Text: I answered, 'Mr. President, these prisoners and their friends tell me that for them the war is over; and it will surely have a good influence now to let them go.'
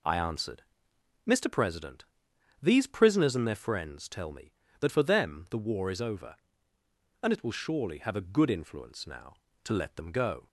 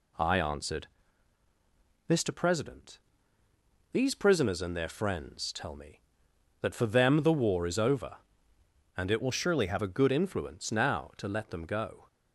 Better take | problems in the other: first | changes voice from "will" to "have"; from 9.2 to 9.7 s; 0.5 s long

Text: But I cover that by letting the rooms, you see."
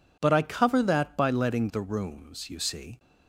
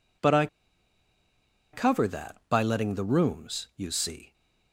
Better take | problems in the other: first | pauses between "I" and "cover"; strong; at 0.4 s; 1.2 s long

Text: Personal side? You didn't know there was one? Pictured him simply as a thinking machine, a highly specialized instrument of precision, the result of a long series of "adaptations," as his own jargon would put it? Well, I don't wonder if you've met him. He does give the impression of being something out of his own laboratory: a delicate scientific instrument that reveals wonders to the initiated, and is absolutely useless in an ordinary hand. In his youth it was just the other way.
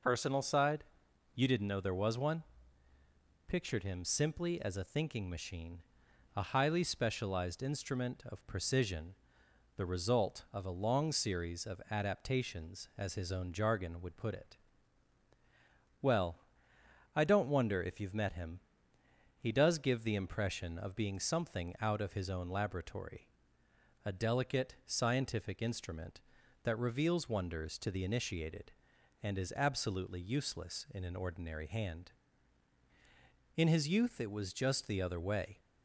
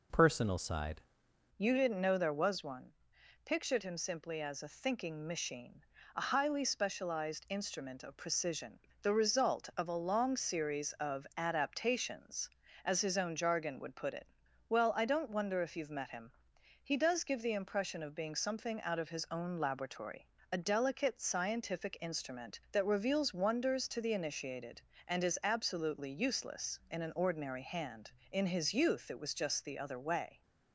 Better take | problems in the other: first | changes voice at "You"; from 1.5 s on; 28.9 s long

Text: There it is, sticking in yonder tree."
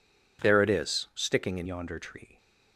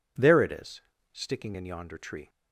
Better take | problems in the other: second | changes voice at "yonder"; from 1.6 s on; 0.7 s long

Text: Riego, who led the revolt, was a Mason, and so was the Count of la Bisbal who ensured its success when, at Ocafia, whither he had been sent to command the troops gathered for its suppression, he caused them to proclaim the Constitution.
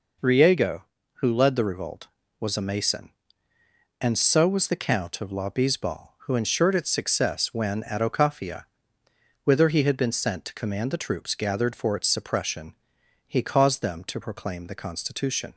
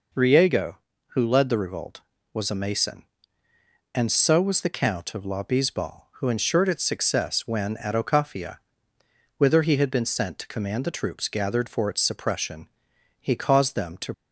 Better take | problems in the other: first | stops before "proclaim the Constitution"; at 14.1 s

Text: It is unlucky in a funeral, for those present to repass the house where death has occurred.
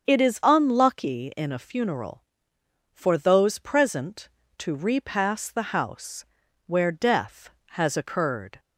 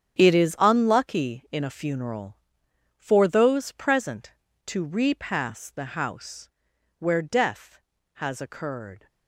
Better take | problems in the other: first | gets quieter; strong; throughout; 12 dB // starts louder than the rest; strong; until 1.1 s; 8 dB; strong in the first // pauses between "house" and "where"; noticeable; at 6.4 s; 0.48 s long; also in the first

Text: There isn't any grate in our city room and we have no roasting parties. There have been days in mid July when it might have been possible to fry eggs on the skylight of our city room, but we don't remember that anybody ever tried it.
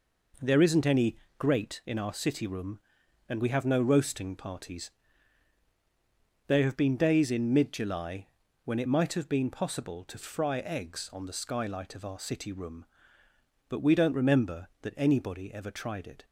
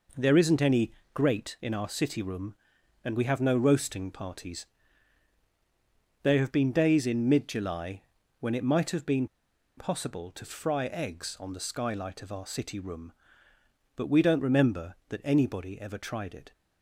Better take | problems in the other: first | pauses between "any" and "grate"; slight; at 0.9 s; 0.22 s long; slight in the first // pauses between "July" and "when"; at 8.0 s; 0.38 s long; also in the first // pauses between "been" and "possible"; noticeable; at 9.2 s; 0.50 s long

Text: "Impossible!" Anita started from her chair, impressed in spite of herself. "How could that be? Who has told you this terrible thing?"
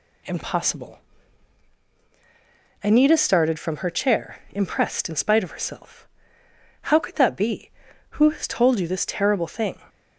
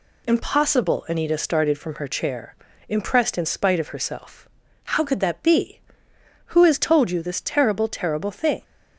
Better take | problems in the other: first | says "terrible" twice; at 7.8 s

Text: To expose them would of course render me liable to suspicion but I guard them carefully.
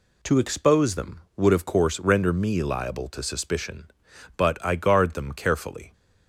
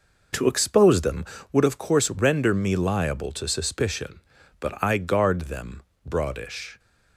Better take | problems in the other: first | says "broadish" for "carefully"; at 6.0 s

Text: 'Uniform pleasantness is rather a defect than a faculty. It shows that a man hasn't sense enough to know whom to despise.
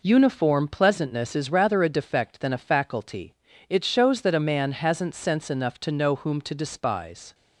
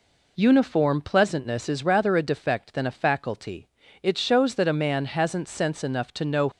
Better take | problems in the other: first | stops before "whom to despise"; at 6.5 s

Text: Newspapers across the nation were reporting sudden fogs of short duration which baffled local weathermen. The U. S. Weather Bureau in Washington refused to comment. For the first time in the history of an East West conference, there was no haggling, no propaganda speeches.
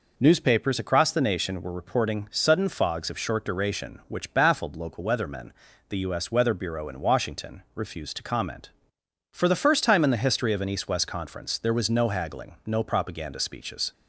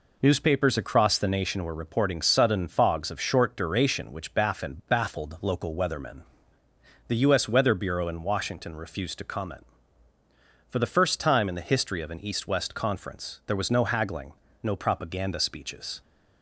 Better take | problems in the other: first | says "baffled" twice; at 4.8 s

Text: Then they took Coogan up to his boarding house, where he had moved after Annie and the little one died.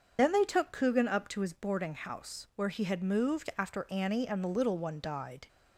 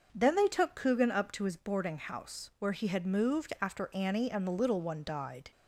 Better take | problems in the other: second | loses the start of "Then"; at 0.1 s; 125 ms // starts louder than the rest; until 1.1 s; 6.5 dB; noticeable in the second

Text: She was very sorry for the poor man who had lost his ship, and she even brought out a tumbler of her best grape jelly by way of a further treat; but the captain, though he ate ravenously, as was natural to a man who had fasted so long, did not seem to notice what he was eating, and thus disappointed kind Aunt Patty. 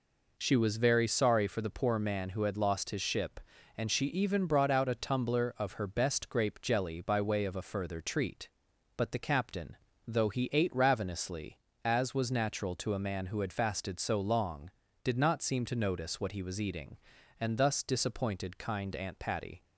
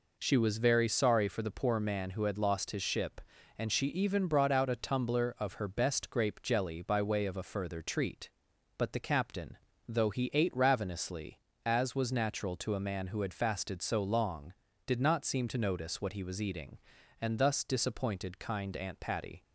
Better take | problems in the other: neither | none

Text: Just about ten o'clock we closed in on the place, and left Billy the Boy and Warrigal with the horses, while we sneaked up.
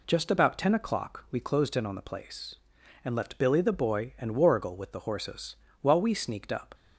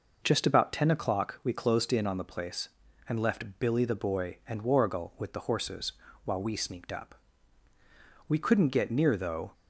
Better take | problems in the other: first | goes on to say "We couldn't get near though"; noticeable; from 8.2 s on; 1.2 s long

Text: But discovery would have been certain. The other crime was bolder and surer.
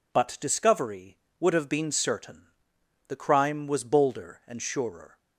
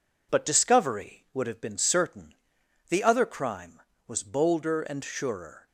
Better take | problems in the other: second | skips "other"; at 3.1 s

